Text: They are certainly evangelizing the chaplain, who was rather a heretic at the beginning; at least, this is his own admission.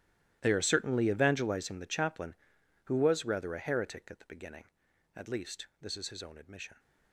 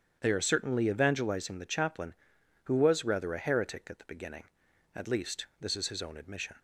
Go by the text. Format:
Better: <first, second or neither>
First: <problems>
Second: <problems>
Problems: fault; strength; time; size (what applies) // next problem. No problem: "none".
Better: second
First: gets quieter; strong; throughout; 17.5 dB // starts louder than the rest; strong; until 1.4 s; 13.5 dB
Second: starts louder than the rest; strong; until 1.2 s; 8.5 dB